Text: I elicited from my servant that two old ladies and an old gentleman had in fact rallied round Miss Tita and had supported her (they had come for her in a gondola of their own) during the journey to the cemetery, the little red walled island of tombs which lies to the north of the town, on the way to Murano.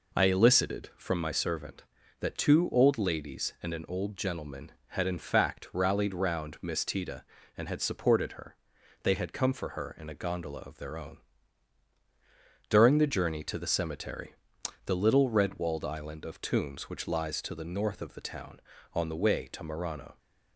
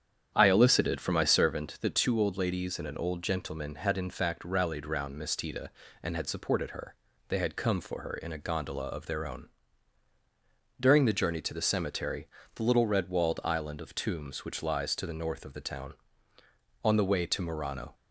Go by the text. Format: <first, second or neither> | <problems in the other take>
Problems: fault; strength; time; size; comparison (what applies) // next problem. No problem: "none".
first | starts louder than the rest; strong; until 1.9 s; 9 dB